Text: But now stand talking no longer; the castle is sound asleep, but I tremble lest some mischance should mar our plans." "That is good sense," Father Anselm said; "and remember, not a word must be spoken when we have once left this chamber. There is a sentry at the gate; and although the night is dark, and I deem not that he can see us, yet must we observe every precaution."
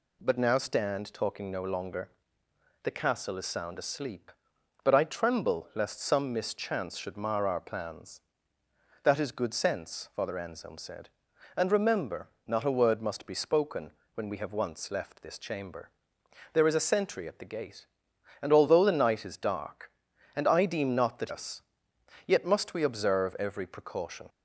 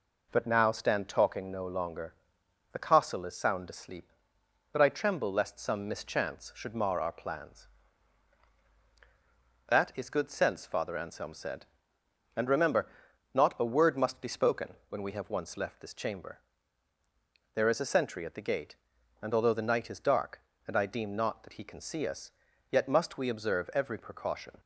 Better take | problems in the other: second | pauses between "spoken" and "when"; slight; at 13.9 s; 0.24 s long // skips "he can see"; at 21.2 s

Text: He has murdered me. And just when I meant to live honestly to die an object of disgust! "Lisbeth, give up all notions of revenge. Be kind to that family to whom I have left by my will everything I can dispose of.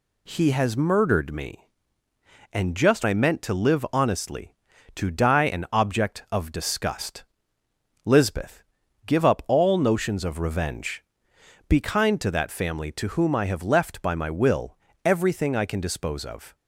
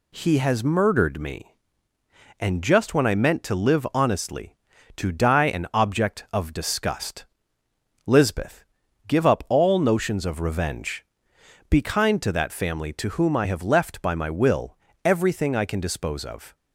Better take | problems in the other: second | skips "when"; at 3.0 s // pauses between "will" and "everything"; slight; at 14.7 s; 0.26 s long; slight in the second

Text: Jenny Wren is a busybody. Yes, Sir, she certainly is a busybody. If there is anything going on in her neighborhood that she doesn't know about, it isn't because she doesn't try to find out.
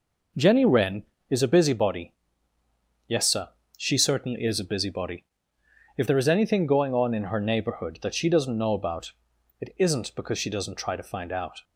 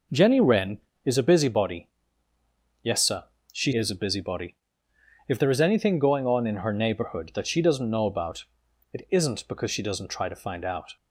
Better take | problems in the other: first | skips "certainly"; at 3.7 s

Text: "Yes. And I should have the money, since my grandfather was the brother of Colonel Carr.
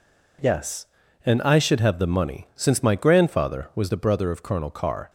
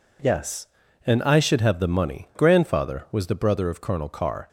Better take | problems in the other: first | skips "since my"; at 2.3 s

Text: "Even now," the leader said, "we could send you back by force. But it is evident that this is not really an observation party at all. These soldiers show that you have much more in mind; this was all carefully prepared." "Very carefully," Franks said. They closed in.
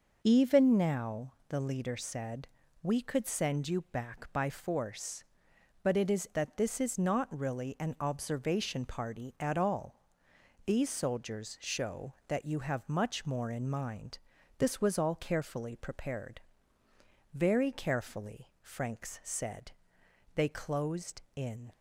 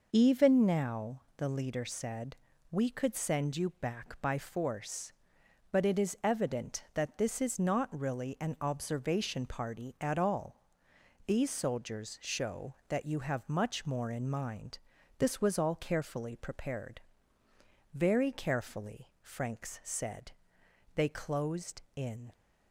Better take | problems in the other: second | skips "evident"; at 6.3 s

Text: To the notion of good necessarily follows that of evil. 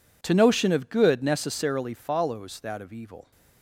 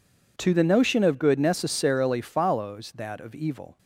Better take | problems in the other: second | skips "the"; at 0.3 s

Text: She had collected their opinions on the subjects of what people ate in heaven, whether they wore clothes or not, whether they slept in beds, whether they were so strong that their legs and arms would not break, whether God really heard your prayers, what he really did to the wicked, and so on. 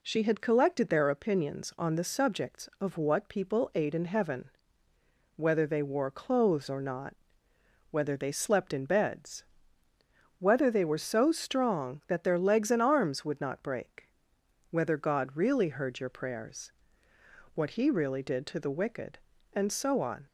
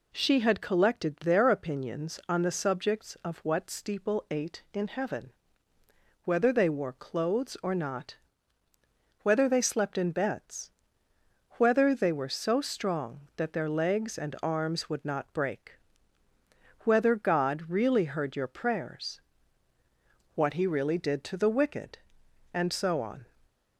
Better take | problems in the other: first | says "steeple" for "people"; at 3.7 s

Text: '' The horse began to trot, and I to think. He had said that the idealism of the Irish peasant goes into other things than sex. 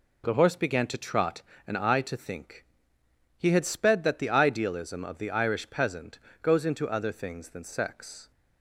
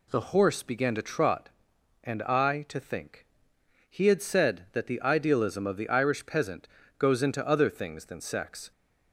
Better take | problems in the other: second | says "sped" for "said"; at 3.6 s // pauses between "peasant" and "goes"; slight; at 6.1 s; 0.24 s long; slight in the second

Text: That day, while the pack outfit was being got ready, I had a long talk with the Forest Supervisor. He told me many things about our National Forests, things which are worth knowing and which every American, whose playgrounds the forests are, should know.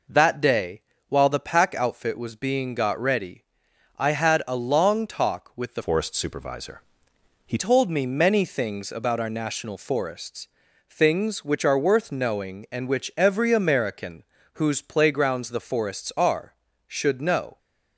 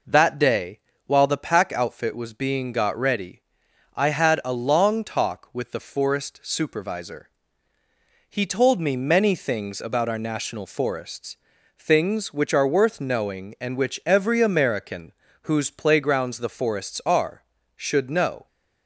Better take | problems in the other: second | changes voice from "Forest" to "He"; from 5.8 to 7.5 s; 1.7 s long

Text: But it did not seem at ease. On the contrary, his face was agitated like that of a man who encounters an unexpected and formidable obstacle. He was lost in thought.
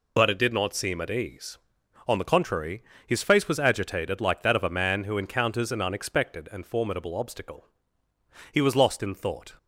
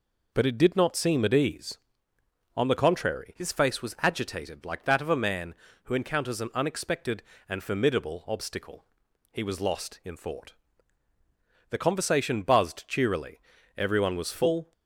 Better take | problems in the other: first | goes on to say "The conversation buzzed cheerily Everyone was full"; strong; from 11.6 s on; 3.0 s long

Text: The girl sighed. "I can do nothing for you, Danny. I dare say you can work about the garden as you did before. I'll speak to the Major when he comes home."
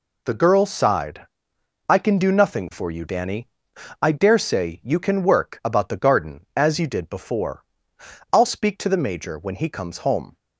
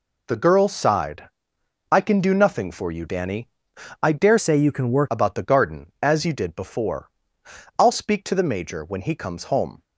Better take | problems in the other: first | changes voice from "say" to "work"; from 4.3 to 5.0 s; 0.7 s long

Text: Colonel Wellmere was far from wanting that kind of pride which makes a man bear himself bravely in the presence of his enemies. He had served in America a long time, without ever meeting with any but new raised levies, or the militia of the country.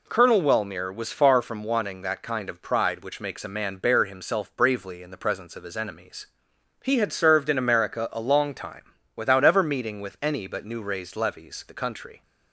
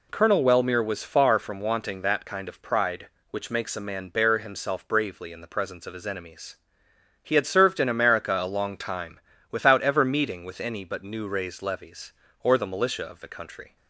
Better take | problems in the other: second | skips "or the militia of"; at 11.6 s

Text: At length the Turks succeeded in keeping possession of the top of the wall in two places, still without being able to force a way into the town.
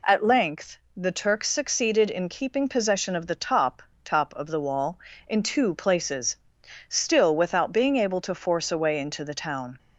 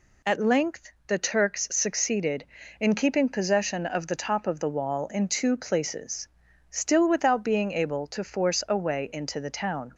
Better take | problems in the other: second | pauses between "length" and "the"; slight; at 0.7 s; 0.22 s long; slight in the second // says "top" twice; at 4.0 s

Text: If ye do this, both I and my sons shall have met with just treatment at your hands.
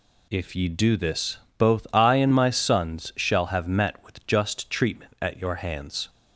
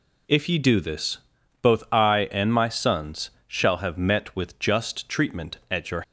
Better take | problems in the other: first | pauses between "sons" and "shall"; slight; at 3.2 s; 0.18 s long // stops before "hands"; at 6.0 s

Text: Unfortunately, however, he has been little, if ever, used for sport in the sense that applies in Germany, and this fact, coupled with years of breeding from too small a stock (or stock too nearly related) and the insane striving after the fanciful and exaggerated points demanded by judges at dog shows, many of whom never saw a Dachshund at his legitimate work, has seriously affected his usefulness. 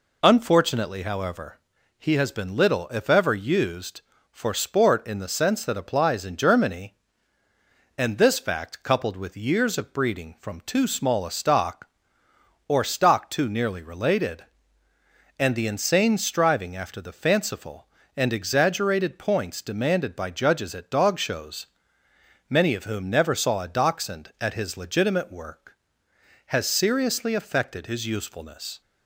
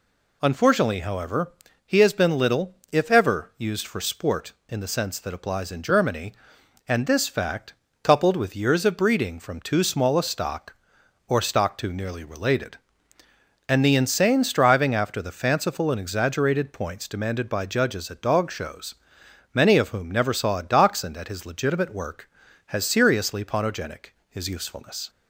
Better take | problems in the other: first | says "ponogenic" for "affected"; at 23.4 s

